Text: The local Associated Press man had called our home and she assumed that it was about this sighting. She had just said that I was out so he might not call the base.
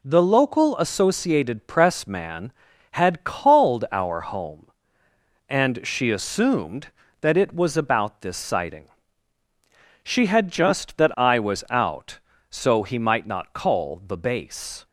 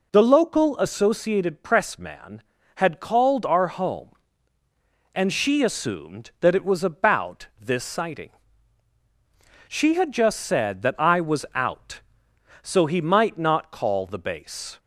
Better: second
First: skips "said"; at 10.9 s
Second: none

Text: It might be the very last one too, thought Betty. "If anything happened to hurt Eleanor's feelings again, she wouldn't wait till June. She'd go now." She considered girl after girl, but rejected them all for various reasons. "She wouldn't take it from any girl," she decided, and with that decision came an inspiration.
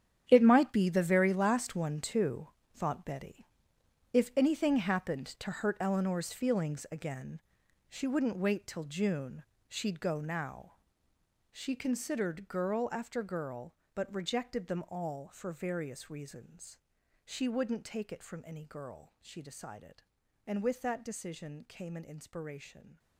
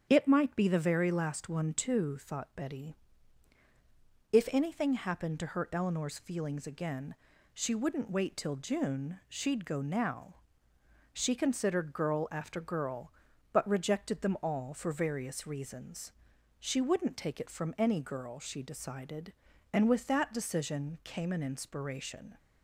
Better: second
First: gets quieter; strong; throughout; 14 dB // starts louder than the rest; strong; until 1.2 s; 9.5 dB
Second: starts louder than the rest; strong; until 1.1 s; 8 dB

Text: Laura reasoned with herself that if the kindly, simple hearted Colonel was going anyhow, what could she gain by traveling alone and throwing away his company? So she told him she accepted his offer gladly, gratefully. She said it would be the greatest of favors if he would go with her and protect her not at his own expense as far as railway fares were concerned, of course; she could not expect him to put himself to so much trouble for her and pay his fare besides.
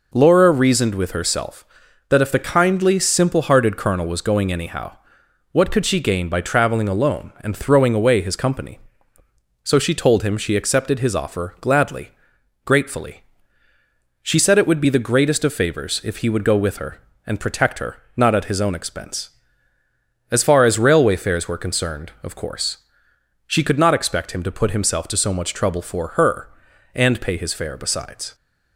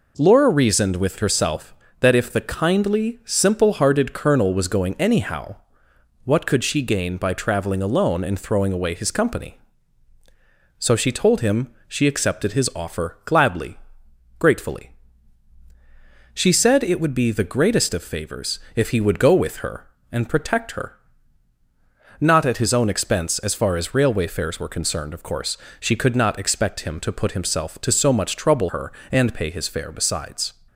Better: first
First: pauses between "her" and "not"; slight; at 17.9 s; 0.20 s long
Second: pauses between "him" and "she"; slight; at 11.6 s; 0.16 s long // pauses between "favors" and "if"; slight; at 18.5 s; 0.16 s long // pauses between "her" and "not"; at 20.9 s; 1.2 s long // skips "for"; at 28.6 s

